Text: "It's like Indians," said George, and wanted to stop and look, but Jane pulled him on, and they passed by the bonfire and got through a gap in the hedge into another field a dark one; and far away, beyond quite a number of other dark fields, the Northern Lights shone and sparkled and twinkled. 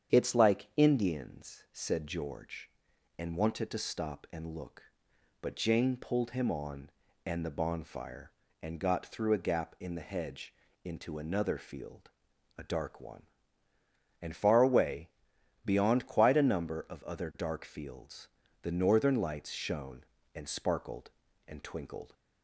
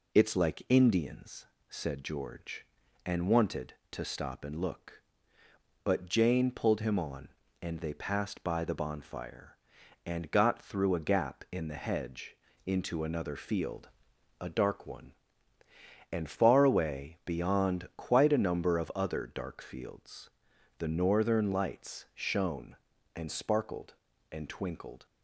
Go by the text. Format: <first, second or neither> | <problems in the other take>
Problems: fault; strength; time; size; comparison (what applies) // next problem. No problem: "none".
second | starts louder than the rest; strong; until 1.1 s; 8 dB // skips "they passed by"; at 7.4 s // pauses between "hedge" and "into"; slight; at 10.5 s; 0.30 s long; slight in the second // pauses between "field" and "a"; noticeable; at 12.0 s; 0.48 s long; noticeable in the second